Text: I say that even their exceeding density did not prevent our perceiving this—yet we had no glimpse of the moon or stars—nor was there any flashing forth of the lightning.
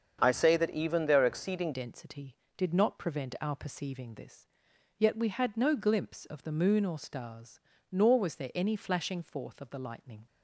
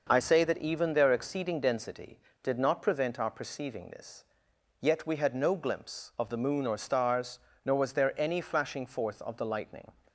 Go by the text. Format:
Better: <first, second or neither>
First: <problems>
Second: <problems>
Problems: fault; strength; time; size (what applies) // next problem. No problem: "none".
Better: second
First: starts louder than the rest; strong; until 1.2 s; 7.5 dB // changes voice at "density"; from 1.7 s on; 8.5 s long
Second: starts louder than the rest; noticeable; until 1.1 s; 6 dB